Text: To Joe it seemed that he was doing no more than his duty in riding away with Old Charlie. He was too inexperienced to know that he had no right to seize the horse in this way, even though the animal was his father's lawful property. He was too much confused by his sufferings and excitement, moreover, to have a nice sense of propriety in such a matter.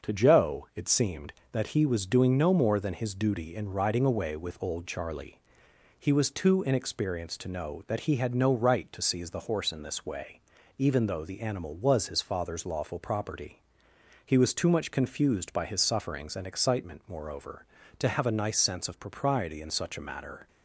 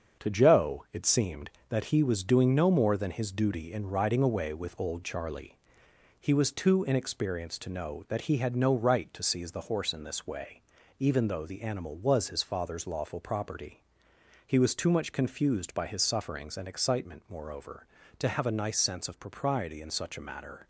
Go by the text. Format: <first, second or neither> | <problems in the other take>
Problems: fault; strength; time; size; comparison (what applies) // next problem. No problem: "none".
first | gets quieter; noticeable; throughout; 5.5 dB // starts louder than the rest; until 1.2 s; 7 dB; also in the first